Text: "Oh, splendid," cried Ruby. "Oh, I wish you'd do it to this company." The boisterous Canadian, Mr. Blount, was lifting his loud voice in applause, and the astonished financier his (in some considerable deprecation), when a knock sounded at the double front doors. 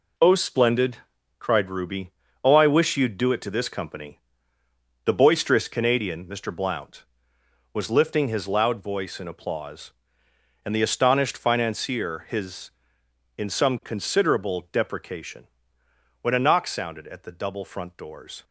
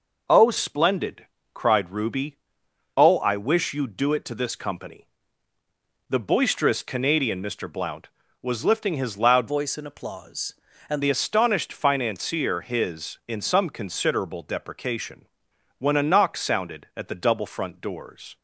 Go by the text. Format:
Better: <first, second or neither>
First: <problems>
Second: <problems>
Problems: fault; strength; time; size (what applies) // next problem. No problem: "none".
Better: first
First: none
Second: changes voice from "voice" to "and"; from 9.4 to 11.0 s; 1.6 s long